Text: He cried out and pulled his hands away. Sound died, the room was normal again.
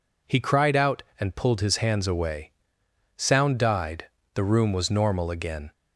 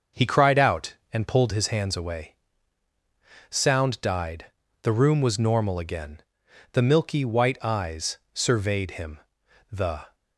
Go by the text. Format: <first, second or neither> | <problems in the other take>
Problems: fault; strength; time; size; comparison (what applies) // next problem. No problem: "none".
first | starts louder than the rest; noticeable; until 1.3 s; 6 dB // goes on to say "The milky white eyes surveyed him the"; strong; from 6.7 s on; 3.4 s long